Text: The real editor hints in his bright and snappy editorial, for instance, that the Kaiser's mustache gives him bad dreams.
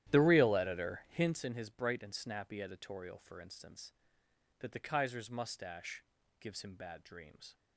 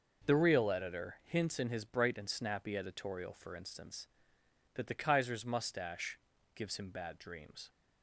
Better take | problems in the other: second | starts louder than the rest; strong; until 1.5 s; 12 dB // pauses between "mustache" and "gives"; at 6.0 s; 0.38 s long; also in the second

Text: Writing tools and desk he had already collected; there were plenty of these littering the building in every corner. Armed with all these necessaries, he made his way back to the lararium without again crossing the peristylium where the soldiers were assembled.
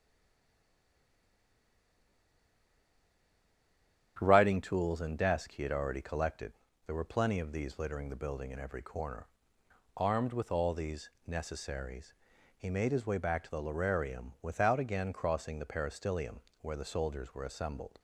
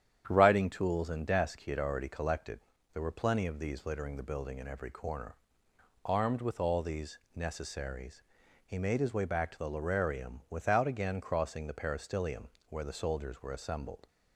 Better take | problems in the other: second | stays silent before the first word; strong; until 4.1 s; 4.1 s long // starts louder than the rest; strong; until 5.2 s; 9.5 dB; strong in the second // pauses between "these" and "necessaries"; slight; at 11.0 s; 0.18 s long; slight in the second // pauses between "peristylium" and "where"; slight; at 16.3 s; 0.22 s long; slight in the second

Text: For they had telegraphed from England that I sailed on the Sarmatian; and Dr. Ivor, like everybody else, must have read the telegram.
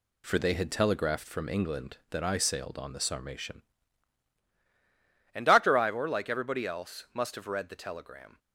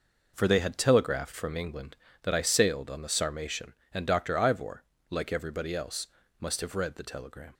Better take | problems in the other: second | changes voice at "and"; from 5.3 s on; 3.0 s long

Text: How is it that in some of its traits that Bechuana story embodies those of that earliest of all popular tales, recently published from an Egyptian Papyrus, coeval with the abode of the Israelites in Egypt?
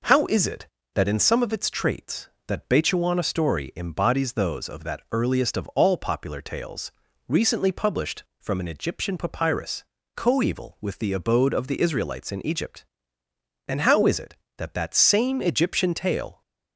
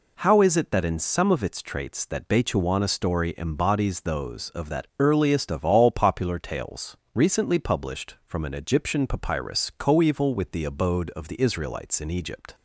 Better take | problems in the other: second | goes on to say "and how is it that that same Egyptian tale"; strong; from 13.6 s on; 2.7 s long

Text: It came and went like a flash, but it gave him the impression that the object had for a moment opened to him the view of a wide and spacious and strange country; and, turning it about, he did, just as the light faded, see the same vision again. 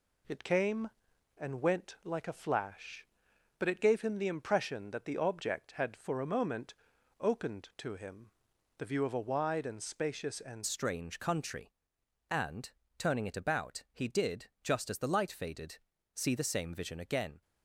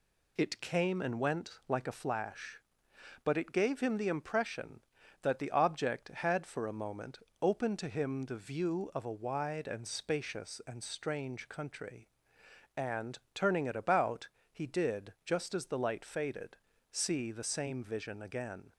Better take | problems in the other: second | pauses between "moment" and "opened"; noticeable; at 6.7 s; 0.46 s long; slight in the second // pauses between "him" and "the"; noticeable; at 8.2 s; 0.52 s long // changes voice at "strange"; from 10.6 s on; 6.8 s long

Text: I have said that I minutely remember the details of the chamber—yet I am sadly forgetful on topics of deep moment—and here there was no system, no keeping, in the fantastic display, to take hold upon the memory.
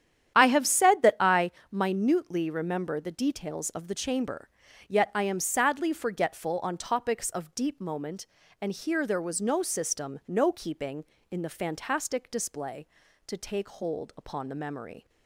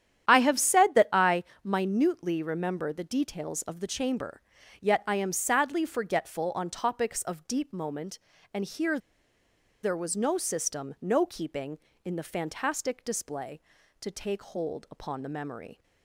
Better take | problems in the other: first | starts louder than the rest; strong; until 1.3 s; 10 dB; strong in the first // pauses between "I" and "minutely"; slight; at 1.4 s; 0.20 s long; slight in the first // pauses between "here" and "there"; noticeable; at 8.9 s; 0.85 s long

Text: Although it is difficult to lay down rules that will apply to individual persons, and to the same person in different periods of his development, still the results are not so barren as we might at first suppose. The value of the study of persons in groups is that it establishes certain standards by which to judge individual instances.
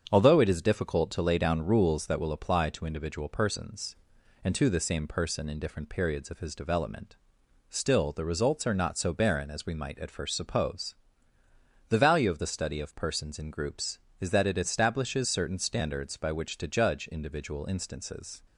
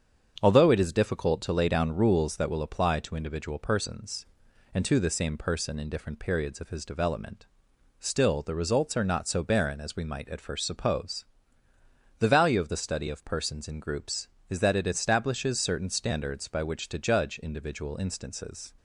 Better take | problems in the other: neither | starts louder than the rest; strong; the same in both

